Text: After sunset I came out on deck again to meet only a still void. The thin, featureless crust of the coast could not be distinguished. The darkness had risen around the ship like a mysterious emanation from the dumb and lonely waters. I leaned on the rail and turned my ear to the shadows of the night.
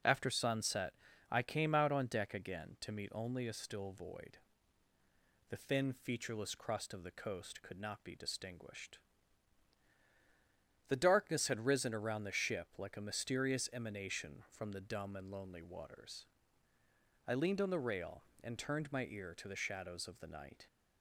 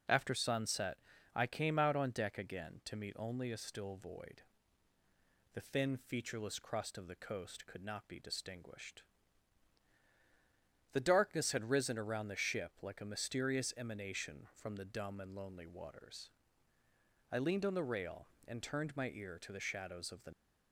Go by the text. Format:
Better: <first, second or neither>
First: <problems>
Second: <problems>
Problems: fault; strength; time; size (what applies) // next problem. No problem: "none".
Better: first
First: pauses between "sunset" and "I"; at 0.9 s; 0.38 s long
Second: pauses between "sunset" and "I"; at 0.9 s; 0.38 s long // stops before "night"; at 20.3 s